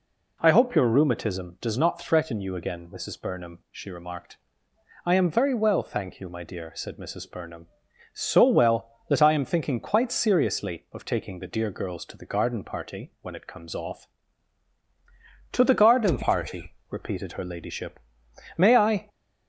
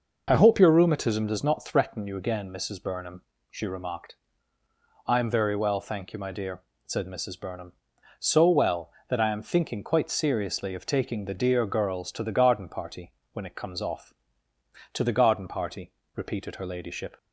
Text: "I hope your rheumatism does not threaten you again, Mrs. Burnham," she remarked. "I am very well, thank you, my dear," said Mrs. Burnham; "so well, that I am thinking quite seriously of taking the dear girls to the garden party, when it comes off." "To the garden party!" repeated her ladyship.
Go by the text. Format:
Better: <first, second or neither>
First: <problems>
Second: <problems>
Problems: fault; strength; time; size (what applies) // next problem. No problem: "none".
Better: second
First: goes on to say "May I"; from 18.5 s on; 0.52 s long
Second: none